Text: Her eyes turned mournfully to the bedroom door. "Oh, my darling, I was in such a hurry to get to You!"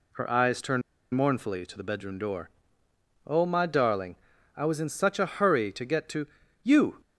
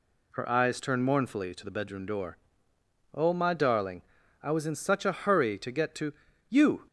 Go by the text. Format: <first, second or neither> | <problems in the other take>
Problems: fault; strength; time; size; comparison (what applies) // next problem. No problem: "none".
second | pauses between "turned" and "mournfully"; slight; at 0.8 s; 0.32 s long // pauses between "to" and "You"; at 6.2 s; 0.38 s long; also in the second